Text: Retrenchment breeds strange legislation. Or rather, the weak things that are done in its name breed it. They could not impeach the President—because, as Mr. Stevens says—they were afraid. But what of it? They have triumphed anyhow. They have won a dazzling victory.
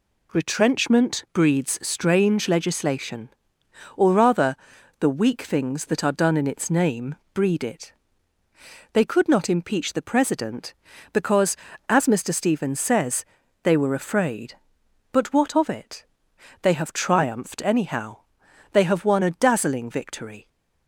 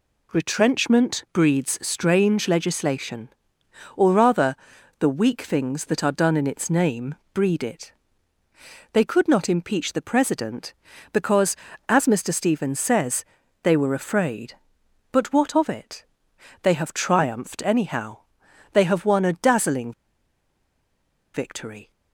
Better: first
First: pauses between "name" and "breed"; slight; at 7.1 s; 0.18 s long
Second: pauses between "name" and "breed"; slight; at 7.1 s; 0.18 s long // pauses between "dazzling" and "victory"; strong; at 19.9 s; 1.4 s long

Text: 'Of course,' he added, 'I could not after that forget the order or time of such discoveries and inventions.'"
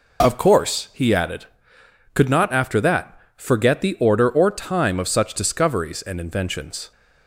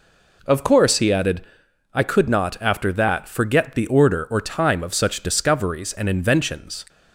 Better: second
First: skips "I"; at 1.7 s // pauses between "that" and "forget"; slight; at 3.1 s; 0.20 s long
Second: none

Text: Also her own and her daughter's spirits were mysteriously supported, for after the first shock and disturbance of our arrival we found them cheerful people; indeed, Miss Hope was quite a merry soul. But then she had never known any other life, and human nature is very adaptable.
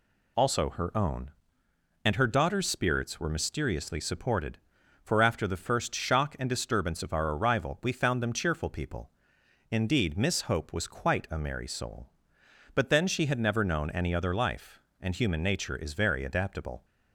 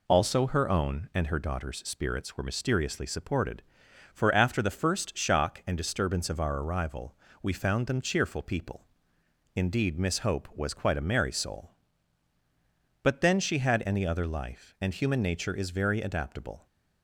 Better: first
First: none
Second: pauses between "arrival" and "we"; slight; at 7.1 s; 0.26 s long // skips "never known"; at 13.8 s

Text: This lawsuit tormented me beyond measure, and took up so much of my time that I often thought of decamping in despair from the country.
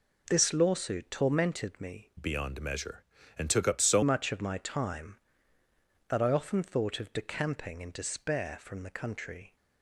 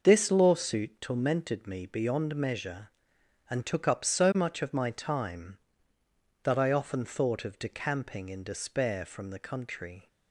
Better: second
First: changes voice from "beyond" to "so"; from 2.1 to 4.0 s; 1.9 s long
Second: none

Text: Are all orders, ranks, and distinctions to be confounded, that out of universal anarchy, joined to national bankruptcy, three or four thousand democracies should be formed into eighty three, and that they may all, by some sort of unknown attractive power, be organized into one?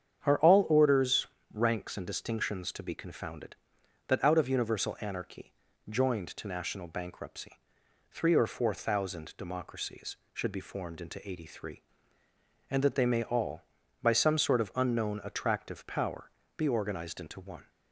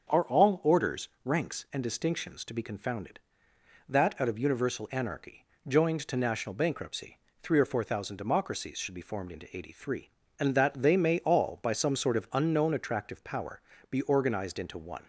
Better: neither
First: starts louder than the rest; strong; until 1.5 s; 8 dB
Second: starts louder than the rest; until 1.2 s; 7 dB

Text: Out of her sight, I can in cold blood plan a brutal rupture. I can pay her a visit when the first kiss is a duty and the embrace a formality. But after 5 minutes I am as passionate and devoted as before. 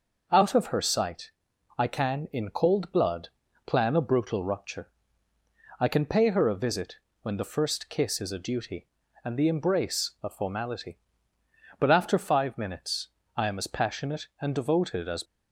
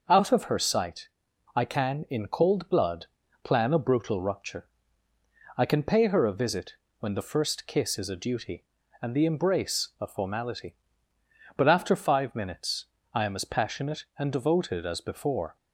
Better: second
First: pauses between "blood" and "plan"; slight; at 3.2 s; 0.36 s long // pauses between "visit" and "when"; slight; at 6.9 s; 0.26 s long // pauses between "minutes" and "I"; slight; at 13.0 s; 0.30 s long // stops before "before"; at 15.2 s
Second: pauses between "blood" and "plan"; slight; at 3.0 s; 0.36 s long // pauses between "visit" and "when"; slight; at 6.7 s; 0.26 s long // pauses between "minutes" and "I"; slight; at 12.8 s; 0.30 s long

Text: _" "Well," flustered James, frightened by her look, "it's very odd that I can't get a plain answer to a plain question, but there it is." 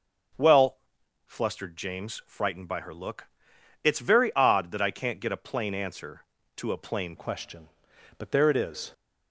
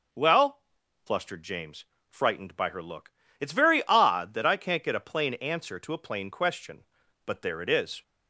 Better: second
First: changes voice at "question"; from 7.1 s on; 1.8 s long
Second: none

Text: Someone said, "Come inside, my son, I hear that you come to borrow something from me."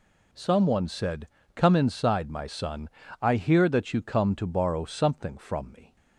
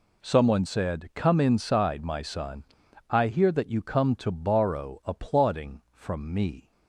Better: first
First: none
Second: says "applauding" for "something"; at 5.0 s

